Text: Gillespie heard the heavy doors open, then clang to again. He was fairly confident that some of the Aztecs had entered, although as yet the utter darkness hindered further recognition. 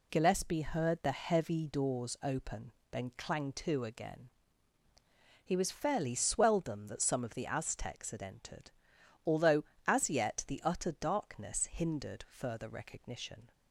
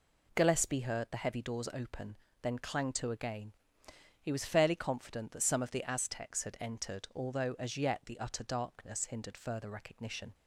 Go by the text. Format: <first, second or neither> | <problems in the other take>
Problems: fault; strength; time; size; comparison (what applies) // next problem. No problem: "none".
second | says "swelldom" for "confident"; at 6.1 s